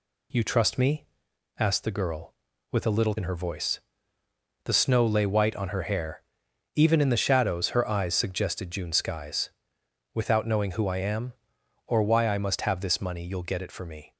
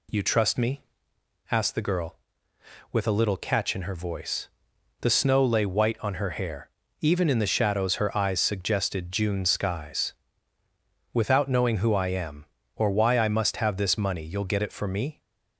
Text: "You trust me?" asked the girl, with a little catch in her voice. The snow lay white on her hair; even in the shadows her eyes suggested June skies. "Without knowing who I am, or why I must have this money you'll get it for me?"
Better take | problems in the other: second | skips "catch"; at 3.1 s

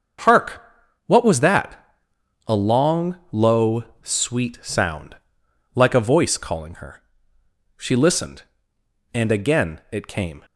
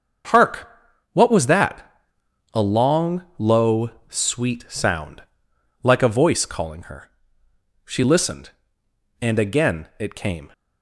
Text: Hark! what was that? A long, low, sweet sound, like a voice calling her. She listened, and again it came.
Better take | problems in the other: neither | starts louder than the rest; the same in both

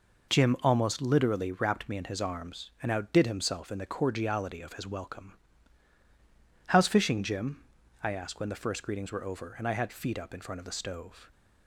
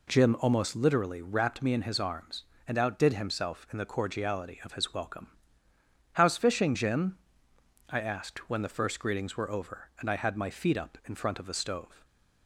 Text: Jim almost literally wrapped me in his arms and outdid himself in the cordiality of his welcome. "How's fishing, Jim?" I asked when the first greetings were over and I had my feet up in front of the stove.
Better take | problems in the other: second | skips "my"; at 9.8 s

